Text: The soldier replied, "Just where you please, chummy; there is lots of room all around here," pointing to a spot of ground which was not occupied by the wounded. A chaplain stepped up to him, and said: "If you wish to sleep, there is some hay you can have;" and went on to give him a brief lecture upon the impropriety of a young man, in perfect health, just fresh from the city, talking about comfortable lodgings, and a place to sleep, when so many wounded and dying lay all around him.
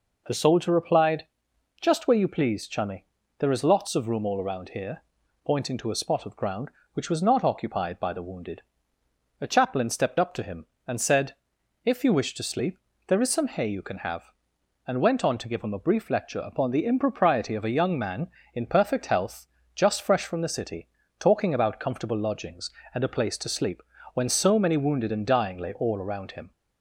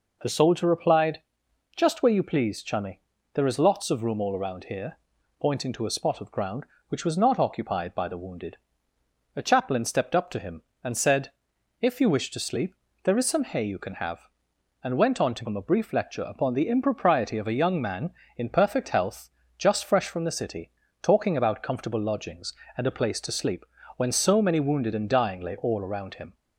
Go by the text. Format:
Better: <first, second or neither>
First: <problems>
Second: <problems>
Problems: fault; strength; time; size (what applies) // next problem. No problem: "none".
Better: first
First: none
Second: skips "give"; at 15.4 s